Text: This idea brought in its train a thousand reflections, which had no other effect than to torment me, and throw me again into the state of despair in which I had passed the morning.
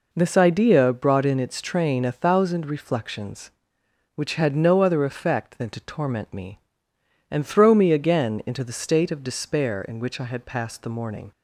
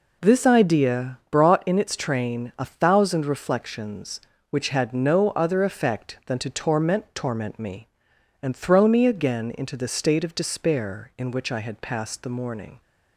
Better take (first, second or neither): first